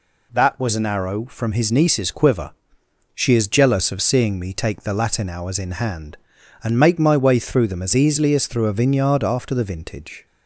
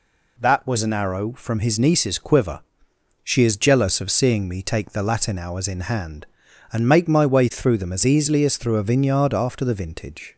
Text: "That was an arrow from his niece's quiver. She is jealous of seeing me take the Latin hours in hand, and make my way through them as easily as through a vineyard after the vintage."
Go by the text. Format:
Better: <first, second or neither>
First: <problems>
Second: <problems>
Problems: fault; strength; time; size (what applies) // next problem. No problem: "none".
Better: neither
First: none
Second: none